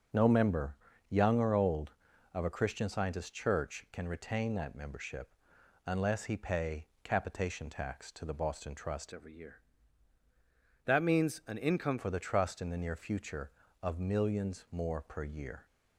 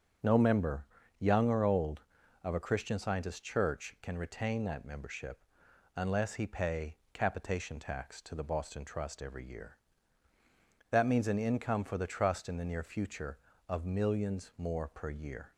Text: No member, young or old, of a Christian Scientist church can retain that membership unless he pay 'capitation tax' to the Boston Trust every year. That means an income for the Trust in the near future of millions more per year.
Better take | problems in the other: second | starts louder than the rest; until 1.4 s; 7 dB; strong in the second // pauses between "membership" and "unless"; noticeable; at 5.2 s; 0.56 s long; noticeable in the second // pauses between "pay" and "capitation"; slight; at 6.8 s; 0.18 s long; slight in the second // changes voice from "every" to "income"; from 9.1 to 11.9 s; 2.8 s long

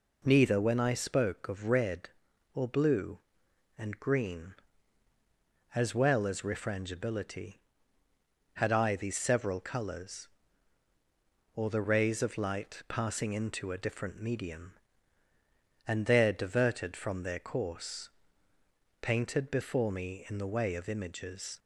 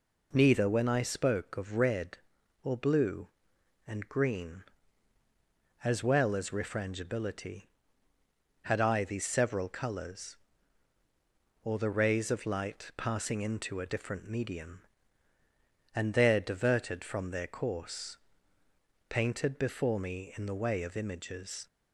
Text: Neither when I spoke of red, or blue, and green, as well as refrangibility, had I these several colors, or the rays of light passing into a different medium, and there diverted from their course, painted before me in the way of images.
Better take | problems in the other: neither | none

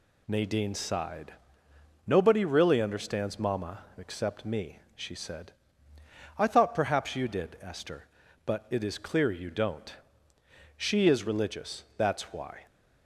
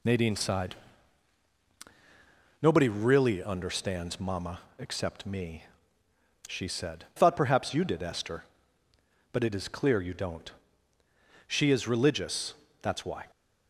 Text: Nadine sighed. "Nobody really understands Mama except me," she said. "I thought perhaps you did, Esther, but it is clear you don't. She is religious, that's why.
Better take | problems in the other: first | pauses between "Mama" and "except"; slight; at 4.5 s; 0.18 s long // skips "I"; at 7.1 s

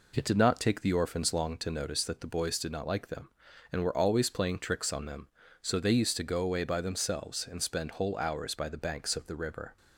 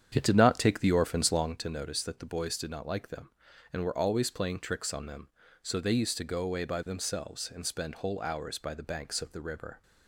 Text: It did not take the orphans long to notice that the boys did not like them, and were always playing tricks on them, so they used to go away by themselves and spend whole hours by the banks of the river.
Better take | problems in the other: first | starts louder than the rest; strong; until 1.7 s; 8.5 dB

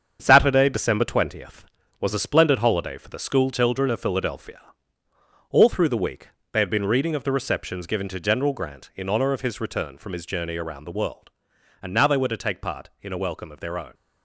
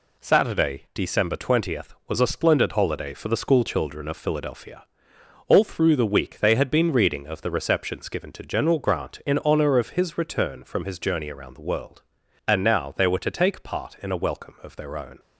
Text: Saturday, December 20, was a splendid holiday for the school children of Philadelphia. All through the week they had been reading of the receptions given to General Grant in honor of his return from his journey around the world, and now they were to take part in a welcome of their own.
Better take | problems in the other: second | gets quieter; throughout; 6.5 dB // pauses between "week" and "they"; slight; at 6.2 s; 0.26 s long

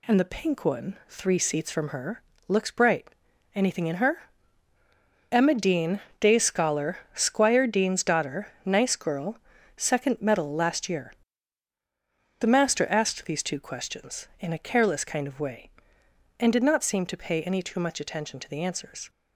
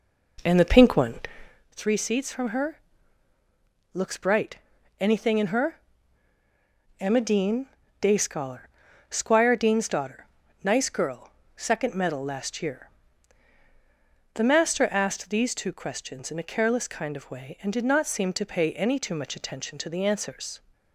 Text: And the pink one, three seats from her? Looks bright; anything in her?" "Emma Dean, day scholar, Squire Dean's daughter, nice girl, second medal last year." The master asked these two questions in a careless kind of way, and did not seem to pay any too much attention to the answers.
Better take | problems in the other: first | starts louder than the rest; noticeable; until 1.6 s; 4.5 dB

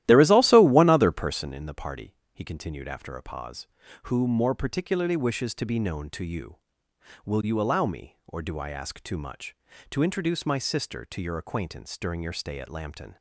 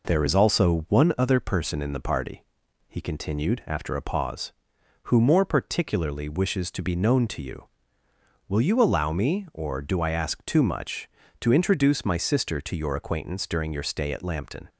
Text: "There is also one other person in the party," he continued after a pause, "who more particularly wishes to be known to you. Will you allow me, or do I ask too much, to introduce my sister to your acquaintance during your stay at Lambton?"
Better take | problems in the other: second | starts louder than the rest; strong; until 1.5 s; 14 dB

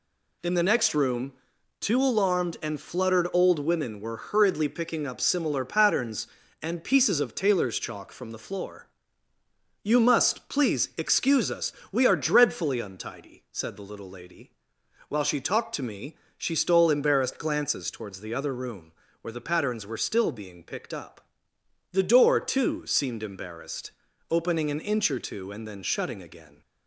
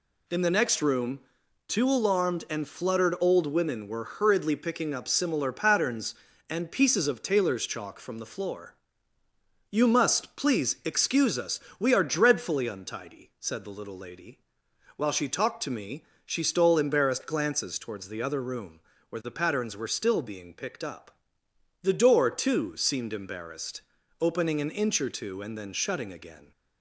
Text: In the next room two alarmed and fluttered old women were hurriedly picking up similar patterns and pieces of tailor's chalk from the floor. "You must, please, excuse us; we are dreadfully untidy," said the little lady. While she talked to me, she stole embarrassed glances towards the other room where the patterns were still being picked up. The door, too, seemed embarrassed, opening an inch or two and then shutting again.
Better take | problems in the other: neither | pauses between "room" and "two"; noticeable; the same in both // pauses between "room" and "where"; slight; the same in both

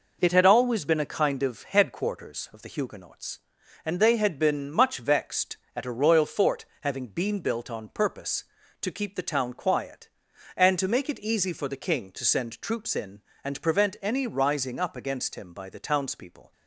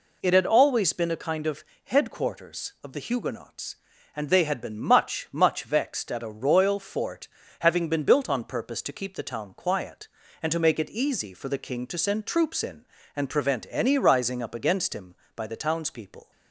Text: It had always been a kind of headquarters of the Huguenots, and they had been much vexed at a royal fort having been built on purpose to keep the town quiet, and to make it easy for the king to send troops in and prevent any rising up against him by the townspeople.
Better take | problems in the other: first | pauses between "of" and "headquarters"; slight; at 1.6 s; 0.20 s long // says "much" twice; at 5.3 s // pauses between "fort" and "having"; slight; at 7.2 s; 0.34 s long; slight in the first

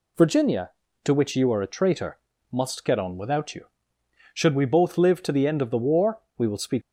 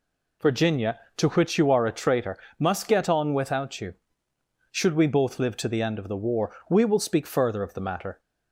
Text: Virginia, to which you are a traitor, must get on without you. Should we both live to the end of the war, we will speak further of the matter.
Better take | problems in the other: second | stops before "further of the matter"; at 6.8 s

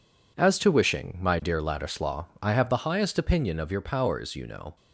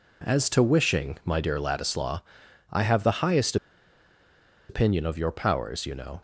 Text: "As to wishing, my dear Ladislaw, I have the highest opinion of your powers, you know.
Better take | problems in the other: first | pauses between "highest" and "opinion"; at 3.5 s; 1.1 s long

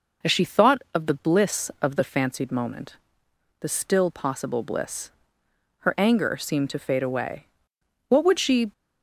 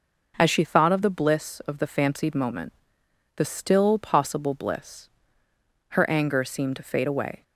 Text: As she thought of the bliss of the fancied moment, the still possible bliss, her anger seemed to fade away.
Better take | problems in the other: second | goes on to say "What would she"; noticeable; from 8.0 s on; 0.64 s long

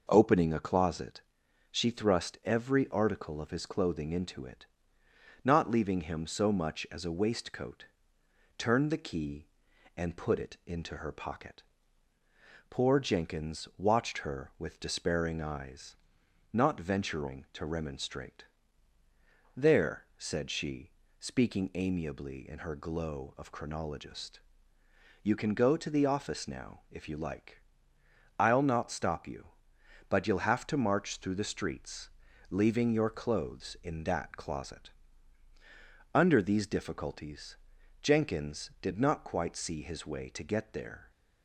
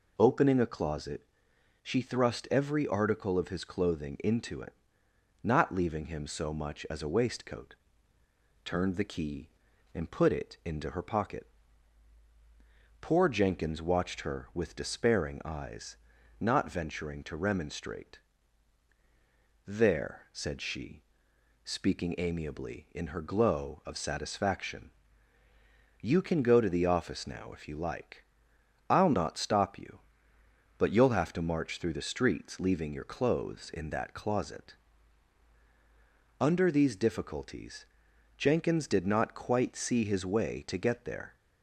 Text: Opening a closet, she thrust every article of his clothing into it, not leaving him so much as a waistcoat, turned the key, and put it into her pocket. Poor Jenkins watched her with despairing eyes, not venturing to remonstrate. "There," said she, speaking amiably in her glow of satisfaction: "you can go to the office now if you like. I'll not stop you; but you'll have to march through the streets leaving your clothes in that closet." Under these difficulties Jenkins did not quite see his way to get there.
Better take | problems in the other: second | says "chronologist" for "satisfaction"; at 23.5 s // pauses between "streets" and "leaving"; at 32.0 s; 0.42 s long // pauses between "difficulties" and "Jenkins"; noticeable; at 37.5 s; 0.46 s long; noticeable in the second

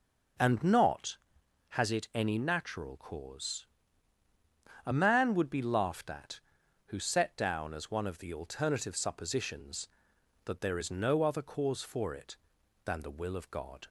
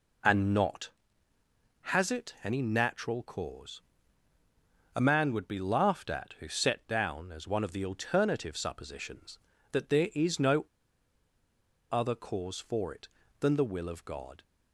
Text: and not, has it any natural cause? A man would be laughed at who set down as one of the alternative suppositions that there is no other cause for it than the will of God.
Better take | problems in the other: first | pauses between "no" and "other"; strong; at 10.6 s; 1.2 s long

